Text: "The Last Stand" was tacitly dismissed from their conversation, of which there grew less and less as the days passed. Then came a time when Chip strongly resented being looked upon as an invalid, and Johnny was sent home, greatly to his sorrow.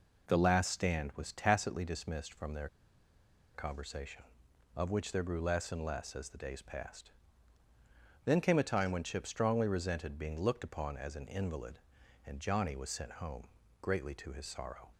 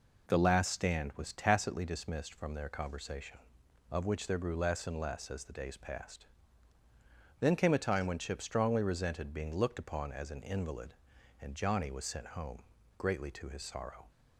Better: second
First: pauses between "their" and "conversation"; noticeable; at 2.6 s; 0.88 s long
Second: none

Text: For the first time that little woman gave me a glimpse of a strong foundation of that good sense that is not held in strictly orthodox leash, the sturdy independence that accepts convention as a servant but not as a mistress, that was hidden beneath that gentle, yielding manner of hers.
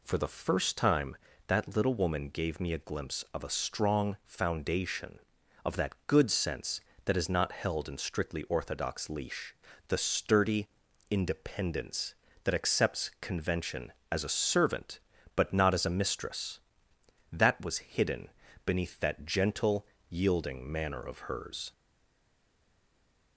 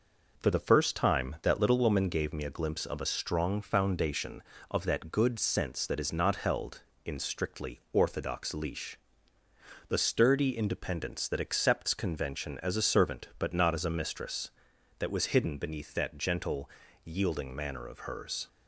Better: second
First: pauses between "sturdy" and "independence"; at 10.6 s; 0.42 s long // pauses between "hidden" and "beneath"; at 18.2 s; 0.38 s long // stays silent after the last word; noticeable; from 21.7 s on; 1.6 s long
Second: none

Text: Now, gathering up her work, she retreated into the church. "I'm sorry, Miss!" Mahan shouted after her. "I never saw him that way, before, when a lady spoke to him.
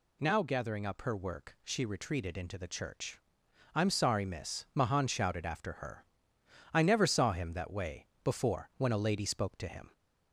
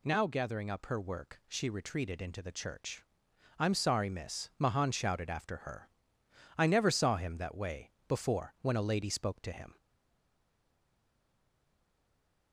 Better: first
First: none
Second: stays silent after the last word; strong; from 9.7 s on; 2.8 s long

